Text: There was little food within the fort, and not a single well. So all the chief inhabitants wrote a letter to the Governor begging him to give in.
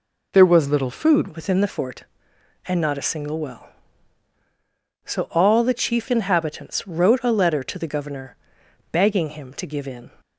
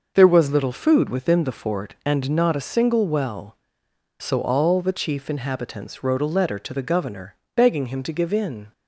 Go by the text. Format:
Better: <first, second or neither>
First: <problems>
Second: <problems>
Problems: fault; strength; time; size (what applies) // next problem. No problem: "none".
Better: second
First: changes voice at "within"; from 1.2 s on; 8.9 s long // pauses between "Governor" and "begging"; noticeable; at 8.3 s; 0.56 s long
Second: pauses between "Governor" and "begging"; slight; at 7.3 s; 0.20 s long